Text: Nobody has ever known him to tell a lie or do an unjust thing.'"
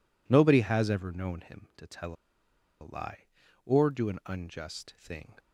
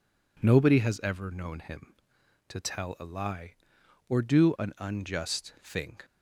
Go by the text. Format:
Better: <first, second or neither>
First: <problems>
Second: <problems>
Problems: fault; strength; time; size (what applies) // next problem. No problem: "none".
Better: second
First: pauses between "tell" and "a"; noticeable; at 2.1 s; 0.67 s long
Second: none